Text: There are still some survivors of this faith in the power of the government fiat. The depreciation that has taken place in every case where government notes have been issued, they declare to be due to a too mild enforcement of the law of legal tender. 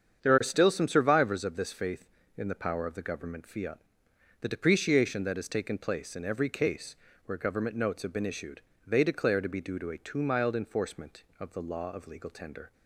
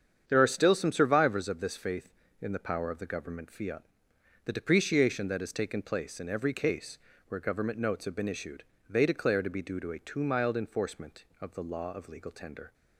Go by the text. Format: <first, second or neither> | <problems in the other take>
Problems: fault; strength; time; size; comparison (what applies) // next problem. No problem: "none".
neither | starts louder than the rest; strong; the same in both // pauses between "case" and "where"; slight; the same in both